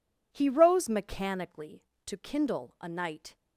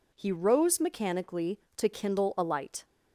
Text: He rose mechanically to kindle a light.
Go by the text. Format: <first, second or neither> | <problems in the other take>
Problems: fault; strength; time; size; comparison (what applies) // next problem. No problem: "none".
second | says "night" for "light"; at 2.8 s